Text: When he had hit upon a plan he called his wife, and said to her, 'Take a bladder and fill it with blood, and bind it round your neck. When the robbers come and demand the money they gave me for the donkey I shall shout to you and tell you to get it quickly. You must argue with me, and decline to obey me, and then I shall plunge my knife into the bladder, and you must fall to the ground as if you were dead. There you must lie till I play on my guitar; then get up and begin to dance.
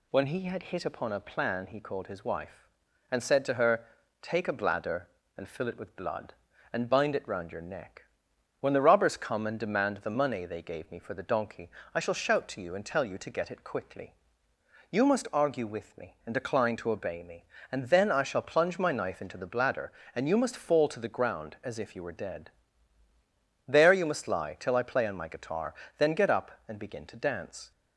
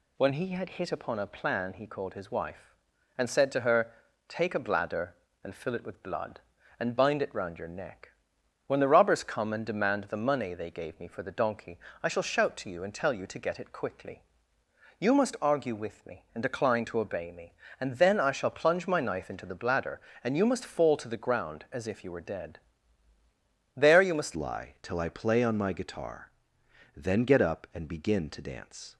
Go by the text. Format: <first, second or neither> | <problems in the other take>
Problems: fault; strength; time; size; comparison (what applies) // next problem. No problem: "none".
first | pauses between "donkey" and "I"; slight; at 11.7 s; 0.24 s long; slight in the first // changes voice at "lie"; from 24.3 s on; 4.6 s long